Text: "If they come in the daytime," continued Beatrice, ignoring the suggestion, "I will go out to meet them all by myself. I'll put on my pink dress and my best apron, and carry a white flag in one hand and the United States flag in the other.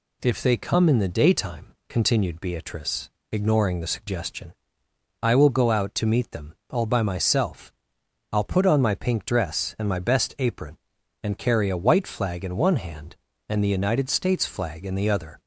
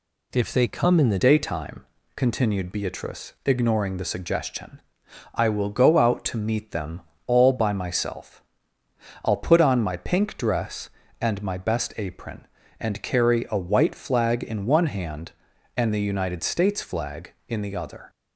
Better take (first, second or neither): first